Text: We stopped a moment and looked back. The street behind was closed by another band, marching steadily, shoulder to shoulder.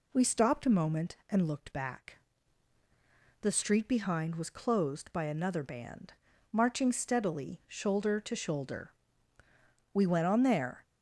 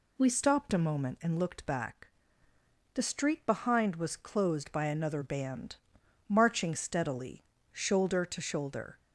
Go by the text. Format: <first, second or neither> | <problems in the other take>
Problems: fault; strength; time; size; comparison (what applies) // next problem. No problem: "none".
second | goes on to say "We went on there"; noticeable; from 9.9 s on; 0.90 s long